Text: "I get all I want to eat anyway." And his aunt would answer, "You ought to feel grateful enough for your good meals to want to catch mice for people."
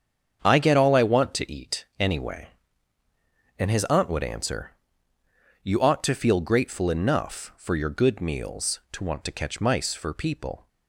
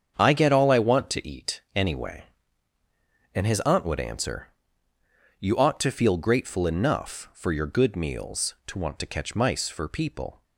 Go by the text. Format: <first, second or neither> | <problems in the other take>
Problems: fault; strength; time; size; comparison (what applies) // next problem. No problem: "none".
neither | starts louder than the rest; strong; the same in both